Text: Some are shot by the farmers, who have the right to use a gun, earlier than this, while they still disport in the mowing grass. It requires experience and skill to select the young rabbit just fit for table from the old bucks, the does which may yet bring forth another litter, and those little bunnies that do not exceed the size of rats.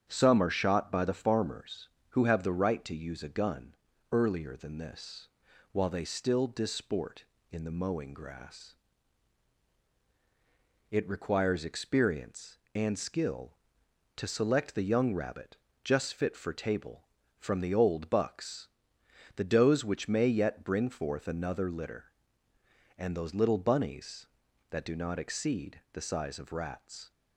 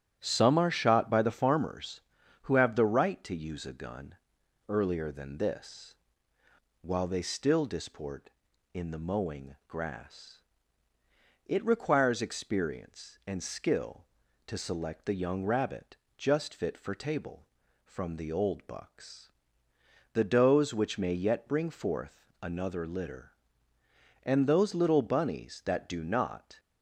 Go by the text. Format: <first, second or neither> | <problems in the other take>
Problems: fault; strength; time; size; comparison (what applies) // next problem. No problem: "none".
first | starts louder than the rest; strong; until 1.2 s; 10.5 dB; strong in the first // pauses between "rabbit" and "just"; slight; at 15.9 s; 0.22 s long; slight in the first // pauses between "forth" and "another"; slight; at 22.2 s; 0.16 s long // stops before "exceed the size of rats"; at 26.5 s